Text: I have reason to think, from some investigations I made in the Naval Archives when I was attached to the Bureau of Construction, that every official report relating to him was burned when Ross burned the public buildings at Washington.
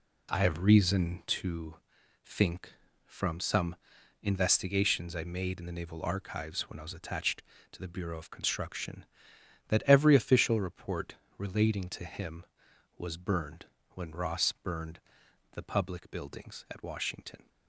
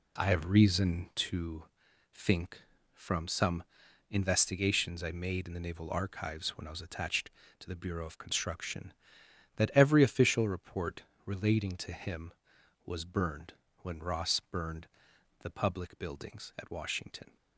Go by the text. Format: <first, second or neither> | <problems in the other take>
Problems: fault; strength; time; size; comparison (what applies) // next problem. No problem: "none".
neither | pauses between "to" and "think"; noticeable; the same in both // pauses between "some" and "investigations"; noticeable; the same in both // pauses between "report" and "relating"; slight; the same in both // pauses between "burned" and "when"; slight; the same in both // pauses between "burned" and "the"; noticeable; the same in both